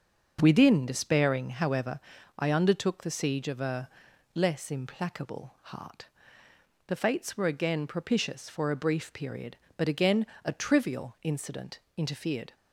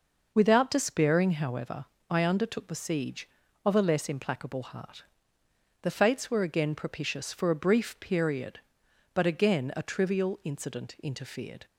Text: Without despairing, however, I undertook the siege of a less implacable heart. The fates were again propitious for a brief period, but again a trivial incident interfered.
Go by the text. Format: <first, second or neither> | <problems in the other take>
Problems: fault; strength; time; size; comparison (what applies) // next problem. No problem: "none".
second | starts louder than the rest; until 1.4 s; 6.5 dB // says "Within" for "Without"; at 0.4 s // pauses between "a" and "less"; at 3.8 s; 0.44 s long // pauses between "again" and "a"; slight; at 10.2 s; 0.20 s long // pauses between "incident" and "interfered"; slight; at 11.7 s; 0.18 s long